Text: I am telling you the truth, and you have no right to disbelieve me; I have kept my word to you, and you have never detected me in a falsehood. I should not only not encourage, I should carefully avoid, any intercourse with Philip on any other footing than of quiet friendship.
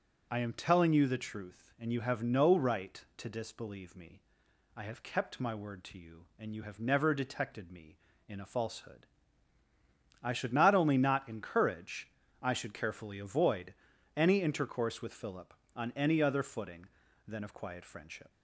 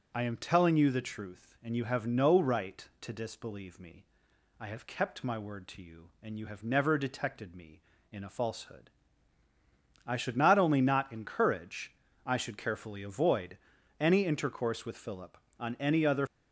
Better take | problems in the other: first | stops before "footing than of quiet friendship"; at 16.2 s

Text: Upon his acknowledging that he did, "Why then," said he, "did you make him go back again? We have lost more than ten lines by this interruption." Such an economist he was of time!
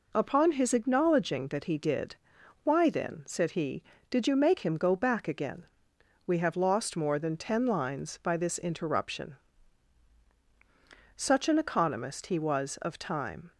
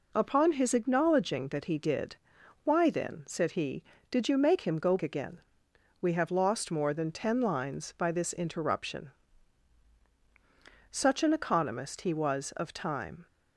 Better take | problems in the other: first | skips "back"; at 4.9 s

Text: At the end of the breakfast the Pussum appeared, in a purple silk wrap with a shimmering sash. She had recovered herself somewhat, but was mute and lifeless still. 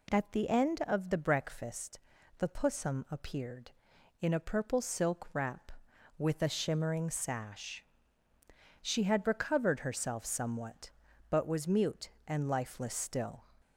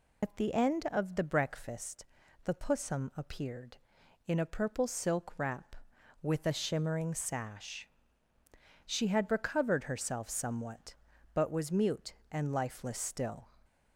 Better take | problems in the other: first | loses the start of "At"; at 0.2 s; 100 ms // pauses between "breakfast" and "the"; at 2.0 s; 0.38 s long; also in the first

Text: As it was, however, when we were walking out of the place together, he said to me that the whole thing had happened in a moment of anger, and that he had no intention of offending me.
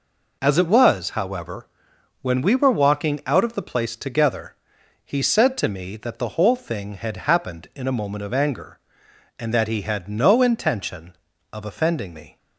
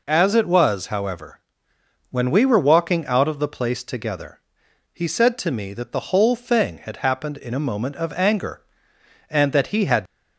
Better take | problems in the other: first | stops before "no intention of offending me"; at 10.0 s

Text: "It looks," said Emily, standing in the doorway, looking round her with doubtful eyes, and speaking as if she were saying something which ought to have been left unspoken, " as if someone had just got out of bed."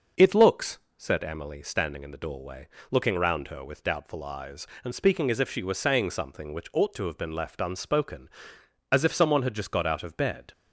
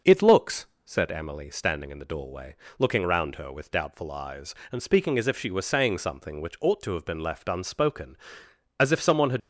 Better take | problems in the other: first | starts louder than the rest; until 1.2 s; 6.5 dB; also in the first // stops before "just got out of bed"; at 9.4 s

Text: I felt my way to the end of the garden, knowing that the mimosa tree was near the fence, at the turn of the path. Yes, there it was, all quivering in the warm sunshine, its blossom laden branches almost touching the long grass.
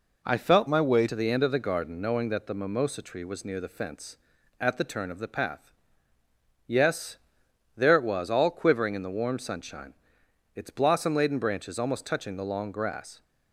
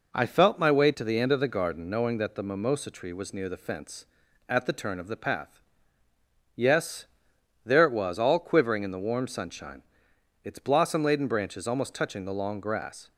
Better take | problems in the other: second | changes voice from "my" to "way"; from 0.6 to 1.0 s; 0.4 s long

